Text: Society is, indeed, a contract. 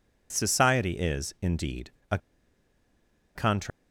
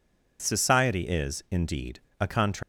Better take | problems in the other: second | pauses between "a" and "contract"; at 2.1 s; 1.1 s long

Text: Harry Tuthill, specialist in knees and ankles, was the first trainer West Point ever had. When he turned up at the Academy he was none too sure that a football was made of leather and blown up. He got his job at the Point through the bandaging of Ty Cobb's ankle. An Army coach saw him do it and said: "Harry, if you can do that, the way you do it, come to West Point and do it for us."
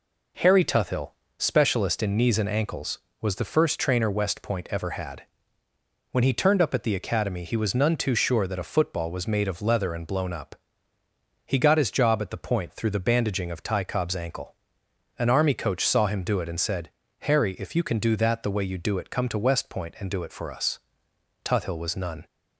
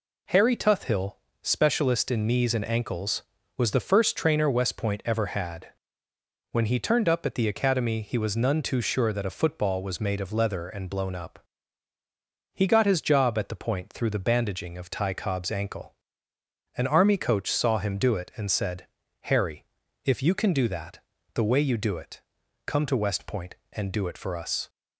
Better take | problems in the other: second | goes on to say "Tuthill was none"; noticeable; from 21.4 s on; 0.82 s long

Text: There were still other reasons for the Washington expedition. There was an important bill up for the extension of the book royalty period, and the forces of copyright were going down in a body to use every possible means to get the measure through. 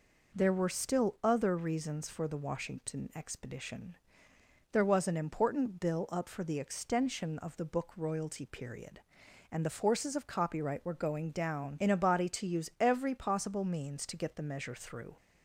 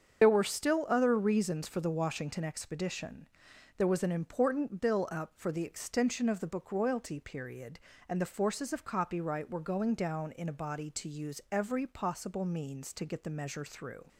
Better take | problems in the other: first | loses the start of "There"; at 0.2 s; 35 ms // starts louder than the rest; until 1.2 s; 7 dB

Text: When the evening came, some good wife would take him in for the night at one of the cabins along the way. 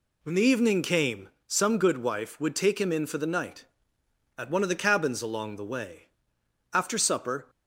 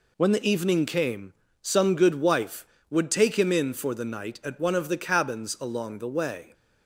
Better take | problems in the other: second | goes on to say "After supper"; noticeable; from 6.7 s on; 0.76 s long

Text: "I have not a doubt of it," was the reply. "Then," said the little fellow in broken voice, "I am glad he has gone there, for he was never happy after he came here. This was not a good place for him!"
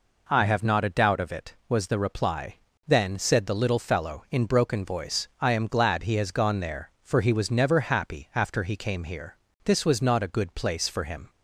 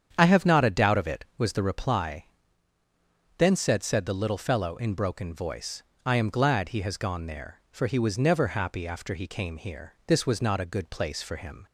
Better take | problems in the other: first | starts louder than the rest; strong; until 1.1 s; 8.5 dB // says "said" twice; at 3.8 s

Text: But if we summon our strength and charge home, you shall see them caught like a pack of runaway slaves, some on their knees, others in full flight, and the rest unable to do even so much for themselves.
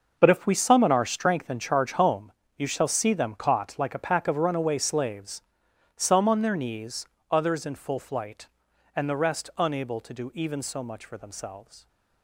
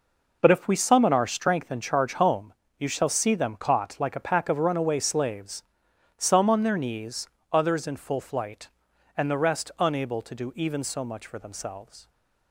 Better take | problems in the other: second | gets quieter; strong; throughout; 13 dB

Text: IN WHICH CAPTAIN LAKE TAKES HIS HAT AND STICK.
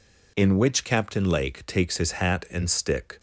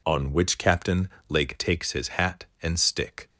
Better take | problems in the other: first | says "On" for "IN"; at 0.0 s // pauses between "CAPTAIN" and "LAKE"; slight; at 1.0 s; 0.20 s long

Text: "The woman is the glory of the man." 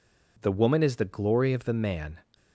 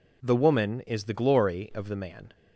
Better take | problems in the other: neither | none

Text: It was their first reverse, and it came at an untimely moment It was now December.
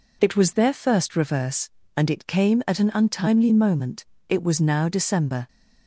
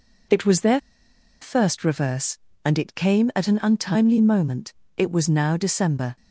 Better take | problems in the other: first | pauses between "their" and "first"; noticeable; at 0.7 s; 0.62 s long // pauses between "moment" and "It"; slight; at 4.7 s; 0.24 s long; slight in the first

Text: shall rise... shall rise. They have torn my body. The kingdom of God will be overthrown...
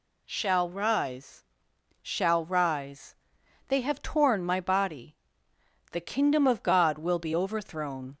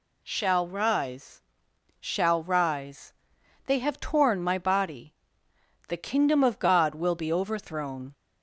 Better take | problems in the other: neither | none

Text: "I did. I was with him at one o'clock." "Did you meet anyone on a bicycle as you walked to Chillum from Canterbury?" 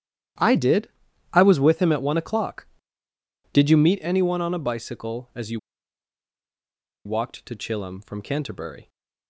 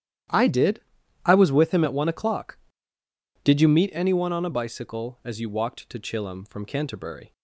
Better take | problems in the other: second | starts louder than the rest; strong; until 1.8 s; 11.5 dB; strong in the second // pauses between "you" and "walked"; strong; at 5.5 s; 1.4 s long

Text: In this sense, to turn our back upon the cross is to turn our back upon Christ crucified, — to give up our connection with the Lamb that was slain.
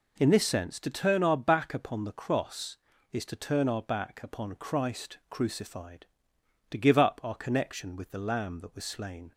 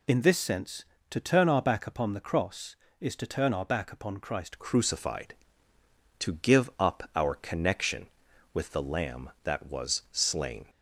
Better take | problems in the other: first | changes voice at "crucified"; from 4.5 s on; 6.1 s long

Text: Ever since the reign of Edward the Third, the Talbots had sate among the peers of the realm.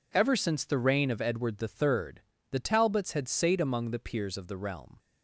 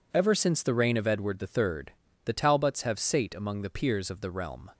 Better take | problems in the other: first | says "have" for "had"; at 2.8 s

